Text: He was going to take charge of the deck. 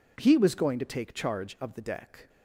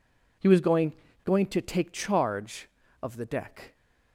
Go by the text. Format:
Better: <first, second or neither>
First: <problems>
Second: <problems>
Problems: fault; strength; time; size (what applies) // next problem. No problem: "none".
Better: first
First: none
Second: says "going" twice; at 1.2 s